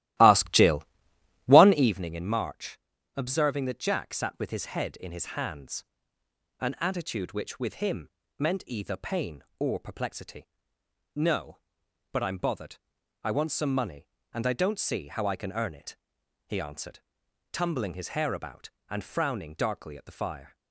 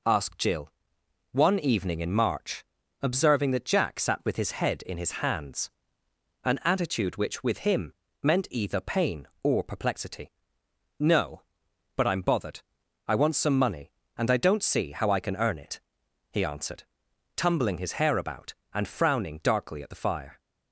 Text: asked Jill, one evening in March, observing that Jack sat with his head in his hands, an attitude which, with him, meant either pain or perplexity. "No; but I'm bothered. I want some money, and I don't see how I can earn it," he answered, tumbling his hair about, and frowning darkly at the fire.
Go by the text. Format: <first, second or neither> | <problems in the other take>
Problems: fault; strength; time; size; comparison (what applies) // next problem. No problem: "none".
second | starts louder than the rest; strong; until 2.0 s; 15 dB